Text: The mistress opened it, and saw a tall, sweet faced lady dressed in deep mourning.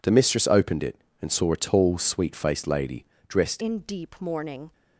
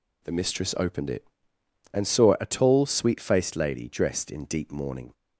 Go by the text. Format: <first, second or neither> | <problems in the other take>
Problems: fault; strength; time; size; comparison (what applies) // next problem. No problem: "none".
second | pauses between "lady" and "dressed"; slight; at 3.0 s; 0.22 s long // changes voice at "in"; from 3.6 s on; 1.1 s long